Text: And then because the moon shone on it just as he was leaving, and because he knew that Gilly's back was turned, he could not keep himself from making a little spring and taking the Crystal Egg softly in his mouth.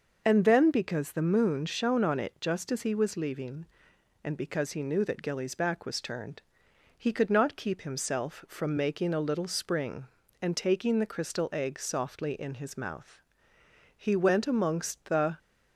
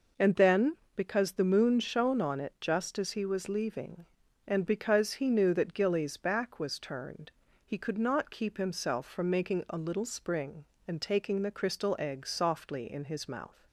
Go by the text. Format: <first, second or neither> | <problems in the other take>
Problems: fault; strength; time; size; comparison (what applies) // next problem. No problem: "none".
second | starts louder than the rest; noticeable; until 1.2 s; 6 dB // goes on to say "He went amongst the"; from 14.0 s on; 1.3 s long